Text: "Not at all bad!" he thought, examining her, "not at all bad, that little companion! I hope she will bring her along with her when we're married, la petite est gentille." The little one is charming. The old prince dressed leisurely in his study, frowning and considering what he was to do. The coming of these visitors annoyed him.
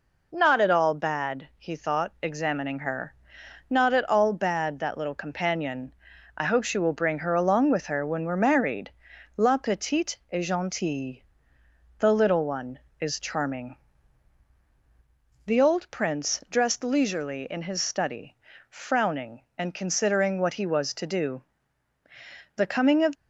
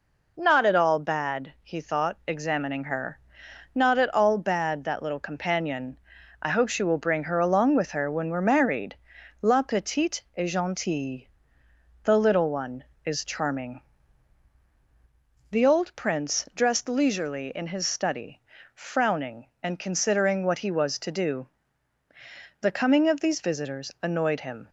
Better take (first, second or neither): second